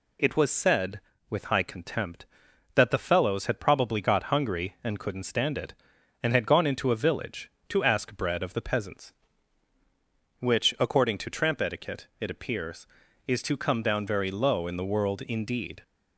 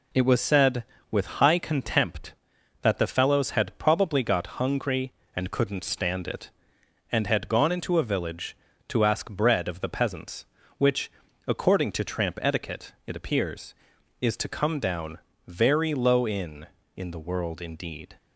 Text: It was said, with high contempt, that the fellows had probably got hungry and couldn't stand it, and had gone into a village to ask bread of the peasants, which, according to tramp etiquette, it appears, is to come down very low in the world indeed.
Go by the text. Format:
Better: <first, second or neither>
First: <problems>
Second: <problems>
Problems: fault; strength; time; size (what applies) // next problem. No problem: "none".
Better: first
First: none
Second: pauses between "down" and "very"; slight; at 15.1 s; 0.28 s long // says "in" twice; at 16.9 s